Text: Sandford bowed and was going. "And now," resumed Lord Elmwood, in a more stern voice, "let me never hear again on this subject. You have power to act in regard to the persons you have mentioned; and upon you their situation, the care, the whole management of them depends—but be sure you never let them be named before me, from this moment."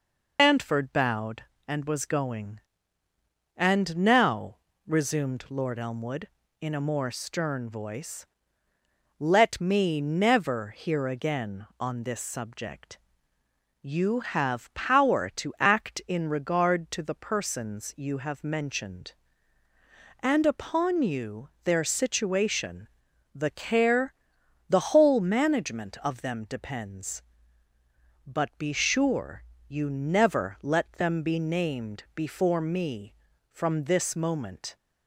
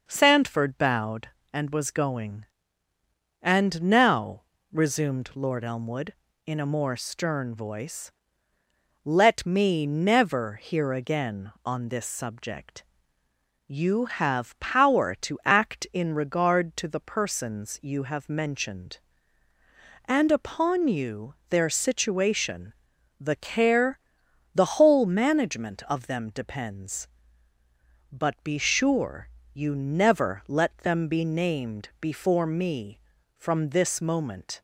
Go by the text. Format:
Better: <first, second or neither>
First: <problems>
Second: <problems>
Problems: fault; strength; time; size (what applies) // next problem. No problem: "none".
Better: second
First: loses the start of "Sandford"; at 0.3 s; 180 ms // pauses between "you" and "their"; slight; at 21.4 s; 0.16 s long // pauses between "sure" and "you"; slight; at 29.4 s; 0.26 s long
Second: pauses between "you" and "their"; slight; at 21.3 s; 0.16 s long // pauses between "sure" and "you"; slight; at 29.2 s; 0.26 s long